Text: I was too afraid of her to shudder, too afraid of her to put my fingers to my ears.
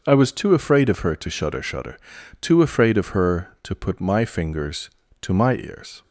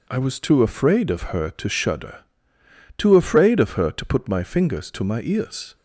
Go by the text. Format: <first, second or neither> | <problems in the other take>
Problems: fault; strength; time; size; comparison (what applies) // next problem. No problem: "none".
second | starts louder than the rest; until 1.0 s; 6.5 dB // says "shudder" twice; at 1.6 s